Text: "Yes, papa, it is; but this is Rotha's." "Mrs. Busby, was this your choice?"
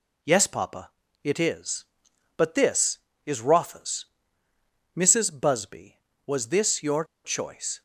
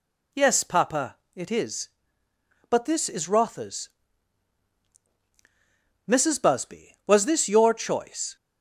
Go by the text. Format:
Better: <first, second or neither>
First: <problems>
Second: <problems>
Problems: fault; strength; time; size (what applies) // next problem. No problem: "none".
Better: second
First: pauses between "your" and "choice"; slight; at 7.0 s; 0.21 s long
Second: none